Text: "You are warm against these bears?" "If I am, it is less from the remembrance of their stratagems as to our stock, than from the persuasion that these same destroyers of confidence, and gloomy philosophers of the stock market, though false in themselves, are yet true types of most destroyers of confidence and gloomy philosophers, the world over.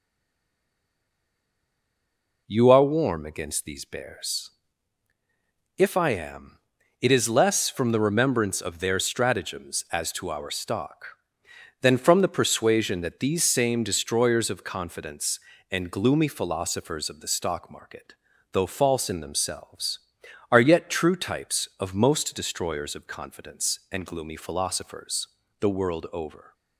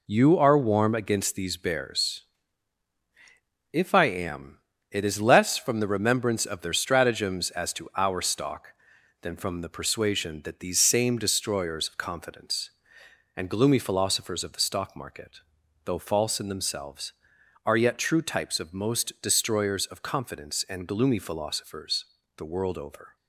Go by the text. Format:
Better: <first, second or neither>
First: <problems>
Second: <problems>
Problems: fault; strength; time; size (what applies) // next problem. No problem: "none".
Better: second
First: stays silent before the first word; until 2.4 s; 2.4 s long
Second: none